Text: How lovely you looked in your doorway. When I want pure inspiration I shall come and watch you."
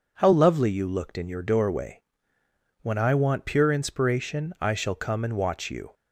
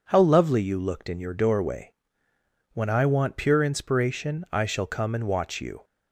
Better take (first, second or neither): neither